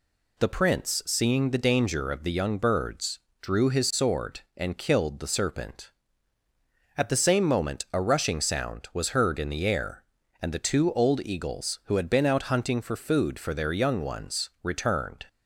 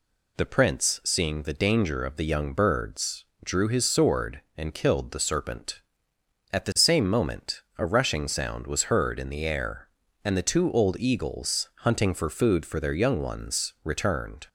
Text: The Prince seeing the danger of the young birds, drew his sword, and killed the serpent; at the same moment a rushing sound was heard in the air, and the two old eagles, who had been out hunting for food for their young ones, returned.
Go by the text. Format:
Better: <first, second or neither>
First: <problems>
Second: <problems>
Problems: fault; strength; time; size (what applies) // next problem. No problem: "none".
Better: first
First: none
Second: pauses between "moment" and "a"; slight; at 7.6 s; 0.16 s long // skips "who had been out"; at 11.7 s